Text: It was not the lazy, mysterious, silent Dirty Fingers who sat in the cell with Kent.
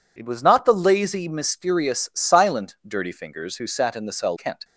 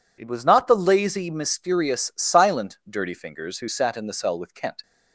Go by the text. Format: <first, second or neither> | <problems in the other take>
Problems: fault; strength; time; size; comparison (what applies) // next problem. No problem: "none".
second | skips "with"; at 4.3 s